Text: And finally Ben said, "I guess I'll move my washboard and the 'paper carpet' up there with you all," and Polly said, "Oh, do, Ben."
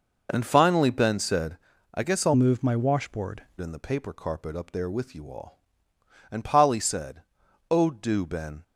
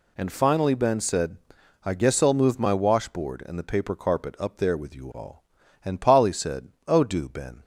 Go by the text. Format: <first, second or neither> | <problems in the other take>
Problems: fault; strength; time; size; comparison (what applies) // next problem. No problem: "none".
second | changes voice from "move" to "washboard"; from 2.3 to 3.4 s; 1.1 s long